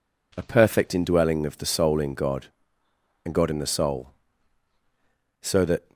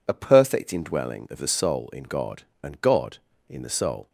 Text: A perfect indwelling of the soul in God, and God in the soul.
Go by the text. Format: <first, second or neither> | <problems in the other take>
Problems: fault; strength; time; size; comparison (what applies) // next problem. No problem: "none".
second | goes on to say "So that"; from 5.4 s on; 0.52 s long